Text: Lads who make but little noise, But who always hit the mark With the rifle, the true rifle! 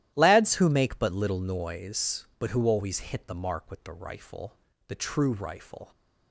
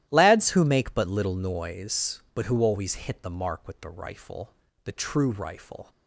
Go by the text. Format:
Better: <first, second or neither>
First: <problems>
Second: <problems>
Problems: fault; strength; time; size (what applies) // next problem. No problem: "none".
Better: neither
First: starts louder than the rest; strong; until 1.1 s; 13.5 dB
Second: starts louder than the rest; strong; until 1.1 s; 13.5 dB